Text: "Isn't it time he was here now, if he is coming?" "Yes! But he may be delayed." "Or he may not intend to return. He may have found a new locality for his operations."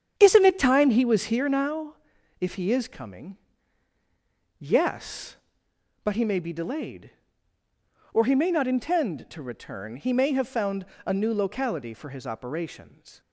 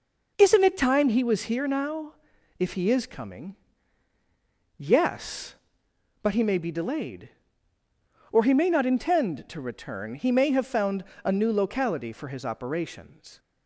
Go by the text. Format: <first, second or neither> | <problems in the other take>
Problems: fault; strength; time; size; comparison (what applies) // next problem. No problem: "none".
second | starts louder than the rest; strong; until 2.0 s; 8.5 dB // pauses between "found" and "a"; slight; at 10.8 s; 0.18 s long; slight in the second